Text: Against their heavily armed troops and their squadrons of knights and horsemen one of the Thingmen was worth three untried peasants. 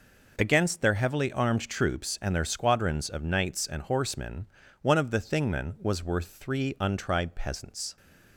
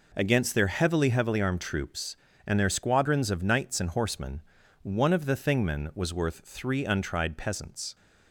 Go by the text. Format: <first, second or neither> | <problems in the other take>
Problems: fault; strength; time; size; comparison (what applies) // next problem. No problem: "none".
first | says "heavily" twice; at 1.0 s // pauses between "horsemen" and "one"; at 4.4 s; 0.42 s long; slight in the first